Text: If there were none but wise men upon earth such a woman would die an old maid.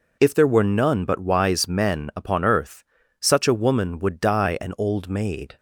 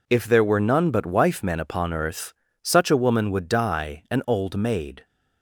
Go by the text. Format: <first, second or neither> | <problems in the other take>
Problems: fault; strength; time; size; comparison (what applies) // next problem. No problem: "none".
first | says "wife" for "wise"; at 1.0 s // pauses between "earth" and "such"; slight; at 2.3 s; 0.30 s long; slight in the first